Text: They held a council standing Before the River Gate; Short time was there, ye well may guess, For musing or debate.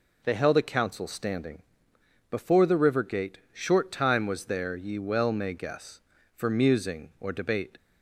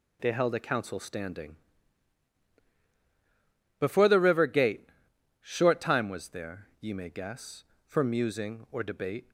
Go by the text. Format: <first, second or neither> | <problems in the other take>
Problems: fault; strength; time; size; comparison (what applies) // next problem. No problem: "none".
first | pauses between "standing" and "Before"; strong; at 1.5 s; 2.2 s long; noticeable in the first // skips "well"; at 6.9 s